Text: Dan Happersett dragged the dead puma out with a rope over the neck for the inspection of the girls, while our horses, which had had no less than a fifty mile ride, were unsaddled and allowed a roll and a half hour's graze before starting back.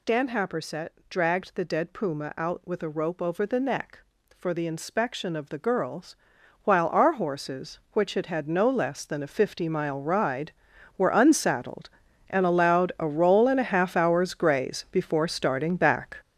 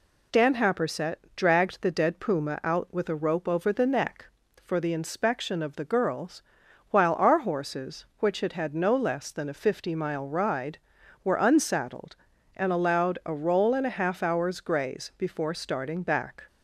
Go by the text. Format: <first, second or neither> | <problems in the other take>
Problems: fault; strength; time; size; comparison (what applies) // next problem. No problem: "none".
second | gets louder; strong; throughout; 8.5 dB // pauses between "Happersett" and "dragged"; slight; at 0.8 s; 0.18 s long; slight in the second